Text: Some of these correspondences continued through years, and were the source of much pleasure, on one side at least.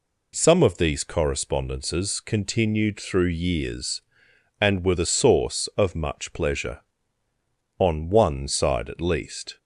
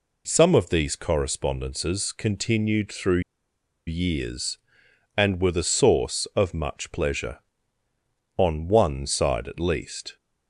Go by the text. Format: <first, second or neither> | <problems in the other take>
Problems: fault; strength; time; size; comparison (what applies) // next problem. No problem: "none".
first | pauses between "through" and "years"; noticeable; at 3.2 s; 0.66 s long